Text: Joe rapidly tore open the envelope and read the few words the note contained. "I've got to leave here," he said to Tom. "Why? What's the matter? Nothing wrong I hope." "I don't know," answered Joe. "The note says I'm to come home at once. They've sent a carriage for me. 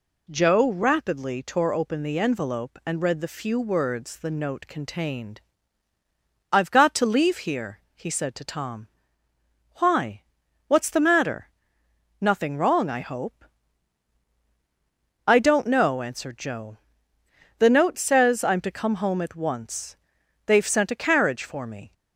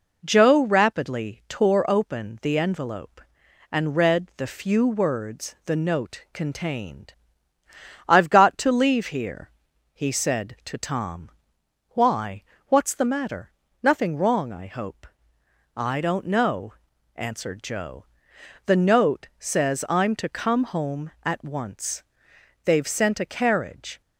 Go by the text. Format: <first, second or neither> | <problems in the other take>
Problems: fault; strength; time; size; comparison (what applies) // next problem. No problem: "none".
first | stops before "for me"; at 24.0 s